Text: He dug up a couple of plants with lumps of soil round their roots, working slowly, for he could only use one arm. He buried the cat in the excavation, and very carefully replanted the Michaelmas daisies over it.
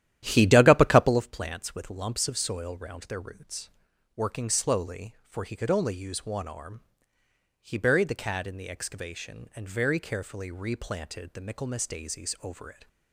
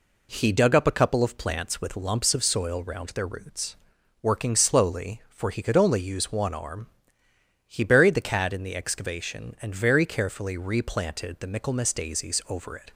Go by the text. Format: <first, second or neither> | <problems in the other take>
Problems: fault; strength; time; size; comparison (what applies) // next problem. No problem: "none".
second | starts louder than the rest; strong; until 1.3 s; 12 dB